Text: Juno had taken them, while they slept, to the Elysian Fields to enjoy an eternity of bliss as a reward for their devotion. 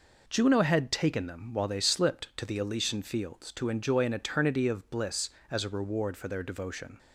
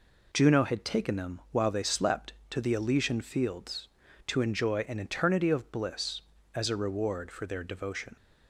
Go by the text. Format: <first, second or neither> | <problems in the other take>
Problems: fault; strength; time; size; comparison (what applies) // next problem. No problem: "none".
second | says "slipped" for "slept"; at 1.7 s